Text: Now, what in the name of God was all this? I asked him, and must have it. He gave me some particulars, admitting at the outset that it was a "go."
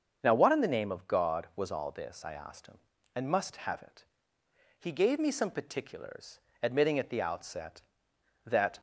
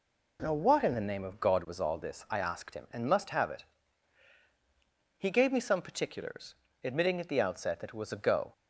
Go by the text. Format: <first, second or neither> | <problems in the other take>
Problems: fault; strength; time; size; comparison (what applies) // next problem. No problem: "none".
second | starts louder than the rest; until 1.2 s; 6.5 dB // stops before "it was a go"; at 8.7 s